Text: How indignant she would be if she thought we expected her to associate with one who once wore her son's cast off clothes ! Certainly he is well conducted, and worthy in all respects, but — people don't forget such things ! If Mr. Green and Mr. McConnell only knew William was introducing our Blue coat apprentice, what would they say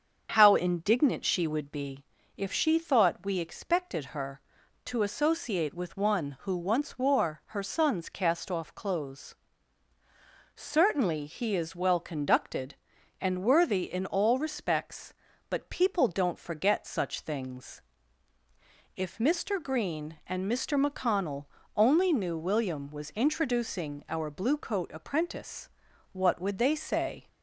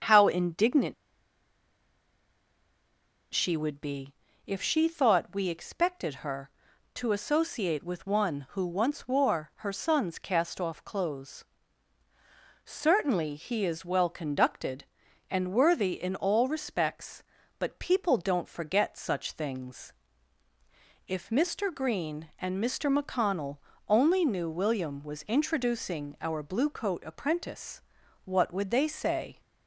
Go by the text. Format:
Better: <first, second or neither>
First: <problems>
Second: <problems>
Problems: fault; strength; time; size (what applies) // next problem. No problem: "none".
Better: first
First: starts louder than the rest; until 1.3 s; 7 dB // pauses between "be" and "if"; slight; at 2.0 s; 0.32 s long // pauses between "McConnell" and "only"; slight; at 21.4 s; 0.28 s long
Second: starts louder than the rest; until 3.4 s; 7 dB // pauses between "indignant" and "she"; strong; at 0.9 s; 2.3 s long // pauses between "be" and "if"; slight; at 4.1 s; 0.32 s long // pauses between "McConnell" and "only"; slight; at 23.5 s; 0.28 s long